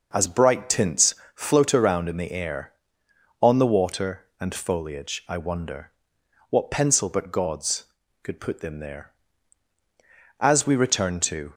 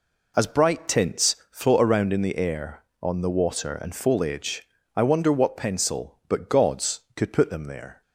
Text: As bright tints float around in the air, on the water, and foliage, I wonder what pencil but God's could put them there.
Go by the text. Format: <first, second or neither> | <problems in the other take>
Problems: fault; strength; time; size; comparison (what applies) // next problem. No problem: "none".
second | pauses between "tints" and "float"; slight; at 1.1 s; 0.20 s long // pauses between "wonder" and "what"; noticeable; at 5.9 s; 0.58 s long // goes on to say "As we return to"; noticeable; from 10.4 s on; 1.1 s long